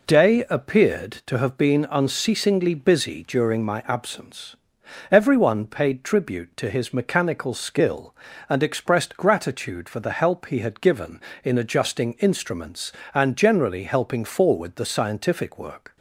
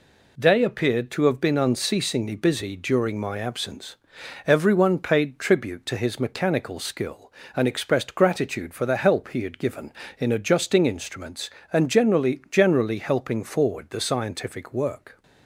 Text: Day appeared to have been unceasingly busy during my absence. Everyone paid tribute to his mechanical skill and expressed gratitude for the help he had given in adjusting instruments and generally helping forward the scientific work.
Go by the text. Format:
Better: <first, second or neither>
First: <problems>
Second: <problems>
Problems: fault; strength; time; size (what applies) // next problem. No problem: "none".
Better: first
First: none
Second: says "generally" twice; at 12.5 s